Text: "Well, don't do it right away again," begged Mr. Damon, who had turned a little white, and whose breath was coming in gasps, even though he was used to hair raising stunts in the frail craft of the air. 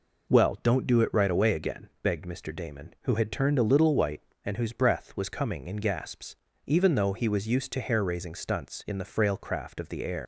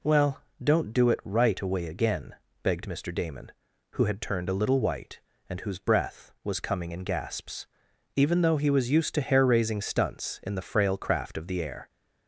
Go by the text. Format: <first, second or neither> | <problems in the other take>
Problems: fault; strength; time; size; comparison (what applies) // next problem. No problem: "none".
second | leaves "air" unfinished; at 10.2 s; 105 ms